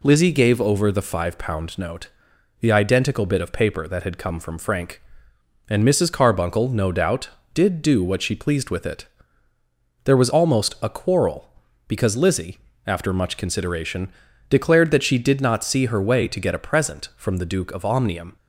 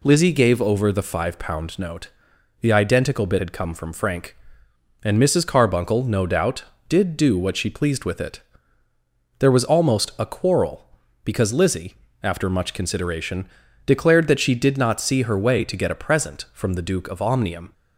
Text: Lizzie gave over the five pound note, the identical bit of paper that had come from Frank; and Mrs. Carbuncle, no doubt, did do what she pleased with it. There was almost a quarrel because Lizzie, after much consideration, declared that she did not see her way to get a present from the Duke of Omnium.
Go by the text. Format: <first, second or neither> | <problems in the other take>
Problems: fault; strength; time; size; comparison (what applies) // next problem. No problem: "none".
first | skips "of paper that"; at 3.3 s